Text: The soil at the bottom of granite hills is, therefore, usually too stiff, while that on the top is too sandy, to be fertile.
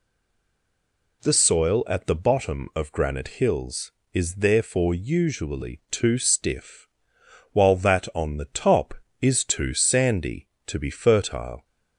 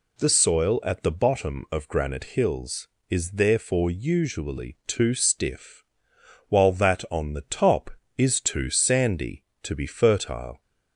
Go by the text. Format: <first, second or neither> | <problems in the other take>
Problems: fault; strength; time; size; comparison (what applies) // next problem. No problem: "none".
second | stays silent before the first word; noticeable; until 1.2 s; 1.2 s long